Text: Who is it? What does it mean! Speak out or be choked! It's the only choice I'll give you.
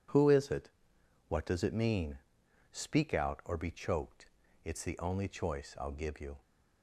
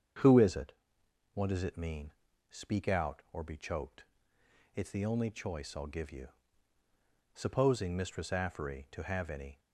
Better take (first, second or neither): first